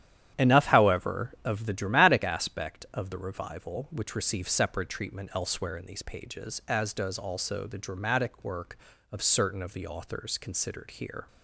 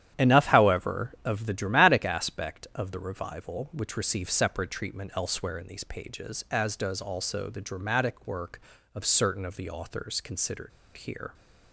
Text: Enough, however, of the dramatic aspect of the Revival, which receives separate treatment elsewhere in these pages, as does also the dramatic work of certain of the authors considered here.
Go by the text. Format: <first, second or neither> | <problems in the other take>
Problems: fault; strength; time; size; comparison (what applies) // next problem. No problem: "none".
first | starts louder than the rest; strong; until 1.2 s; 10.5 dB; strong in the first // pauses between "considered" and "here"; slight; at 10.7 s; 0.26 s long